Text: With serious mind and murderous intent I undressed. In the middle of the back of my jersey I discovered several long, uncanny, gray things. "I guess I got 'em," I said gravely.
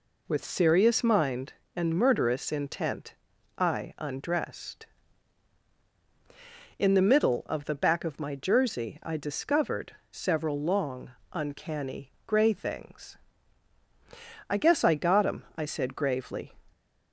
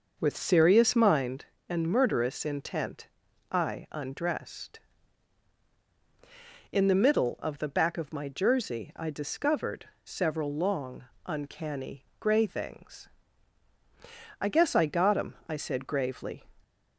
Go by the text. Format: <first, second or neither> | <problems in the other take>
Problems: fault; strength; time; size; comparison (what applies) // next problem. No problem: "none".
first | starts louder than the rest; noticeable; until 1.3 s; 6 dB // pauses between "intent" and "I"; at 3.0 s; 0.44 s long; also in the first // pauses between "discovered" and "several"; slight; at 9.8 s; 0.18 s long; slight in the first